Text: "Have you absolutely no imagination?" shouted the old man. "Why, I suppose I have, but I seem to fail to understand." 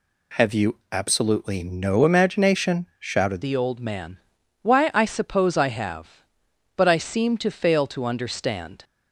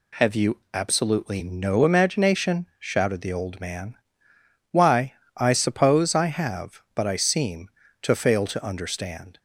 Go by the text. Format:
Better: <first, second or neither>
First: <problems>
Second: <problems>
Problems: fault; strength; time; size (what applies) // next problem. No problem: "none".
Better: second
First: changes voice at "the"; from 3.4 s on; 5.4 s long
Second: none